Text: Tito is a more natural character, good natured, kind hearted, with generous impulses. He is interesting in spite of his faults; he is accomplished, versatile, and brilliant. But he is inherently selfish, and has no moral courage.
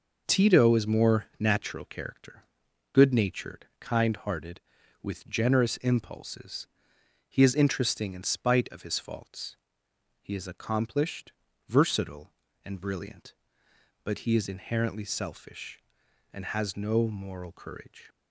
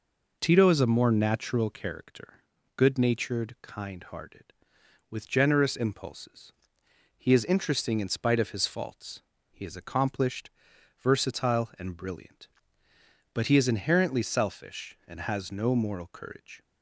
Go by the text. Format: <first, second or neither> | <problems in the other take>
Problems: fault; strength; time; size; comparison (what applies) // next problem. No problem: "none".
second | skips "a"; at 0.8 s